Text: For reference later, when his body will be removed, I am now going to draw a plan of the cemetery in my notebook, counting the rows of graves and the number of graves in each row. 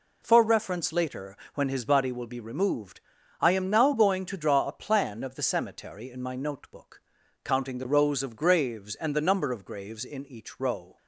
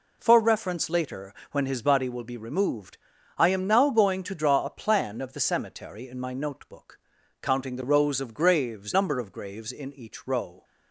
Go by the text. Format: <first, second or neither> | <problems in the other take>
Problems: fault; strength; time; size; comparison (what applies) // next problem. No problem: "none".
first | skips "and the"; at 8.9 s